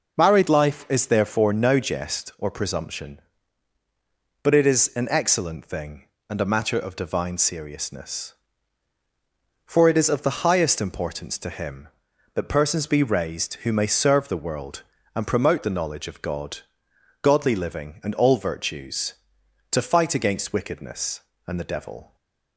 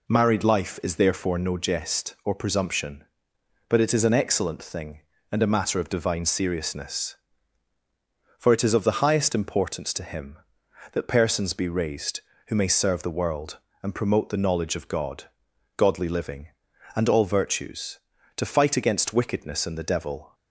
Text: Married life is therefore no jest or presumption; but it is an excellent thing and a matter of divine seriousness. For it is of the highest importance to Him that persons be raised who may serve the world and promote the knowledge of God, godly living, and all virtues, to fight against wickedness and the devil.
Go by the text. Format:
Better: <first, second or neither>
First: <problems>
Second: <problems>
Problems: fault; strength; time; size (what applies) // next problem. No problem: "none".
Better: neither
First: none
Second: none